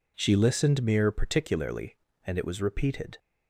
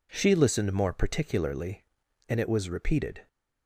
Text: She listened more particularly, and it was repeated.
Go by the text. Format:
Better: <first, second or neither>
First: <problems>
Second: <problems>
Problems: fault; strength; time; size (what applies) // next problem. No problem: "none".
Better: second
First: says "mere" for "more"; at 0.8 s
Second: none